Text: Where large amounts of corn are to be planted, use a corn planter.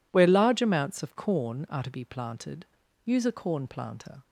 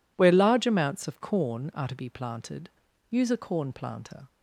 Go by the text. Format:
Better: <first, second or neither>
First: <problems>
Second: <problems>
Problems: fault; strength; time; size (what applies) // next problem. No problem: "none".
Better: neither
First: none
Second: none